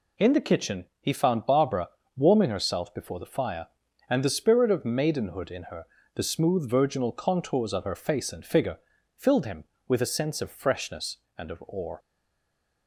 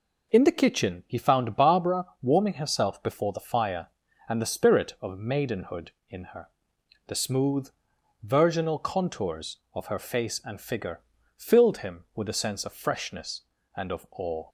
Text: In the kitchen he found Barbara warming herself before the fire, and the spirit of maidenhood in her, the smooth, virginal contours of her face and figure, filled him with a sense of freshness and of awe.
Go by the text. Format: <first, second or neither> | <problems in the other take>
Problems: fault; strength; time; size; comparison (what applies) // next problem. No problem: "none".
second | pauses between "kitchen" and "he"; slight; at 0.8 s; 0.16 s long // pauses between "Barbara" and "warming"; slight; at 1.8 s; 0.26 s long; slight in the second // stays silent after the last word; slight; from 11.9 s on; 0.9 s long